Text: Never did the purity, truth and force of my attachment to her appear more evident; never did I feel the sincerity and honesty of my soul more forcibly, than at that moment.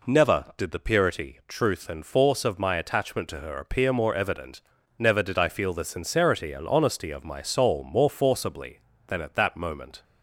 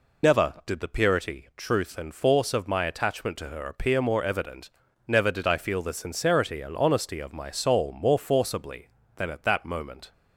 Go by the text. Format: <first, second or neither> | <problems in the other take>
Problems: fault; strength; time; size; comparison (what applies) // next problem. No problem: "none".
first | loses the start of "Never"; at 0.2 s; 125 ms